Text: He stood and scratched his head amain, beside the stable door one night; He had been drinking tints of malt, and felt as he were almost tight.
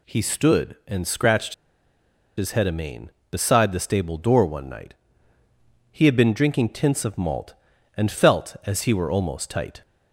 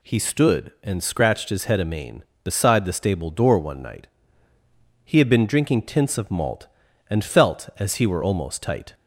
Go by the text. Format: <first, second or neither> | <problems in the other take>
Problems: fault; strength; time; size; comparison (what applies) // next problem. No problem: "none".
second | pauses between "scratched" and "his"; noticeable; at 1.5 s; 0.83 s long